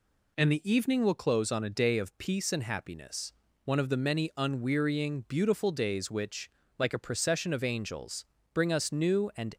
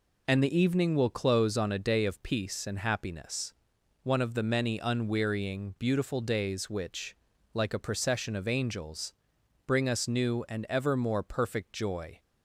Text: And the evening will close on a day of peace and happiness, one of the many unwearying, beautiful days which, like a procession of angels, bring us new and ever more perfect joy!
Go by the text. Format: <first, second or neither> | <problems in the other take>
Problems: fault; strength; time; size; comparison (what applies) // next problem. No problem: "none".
second | stops before "ever more perfect joy"; at 9.5 s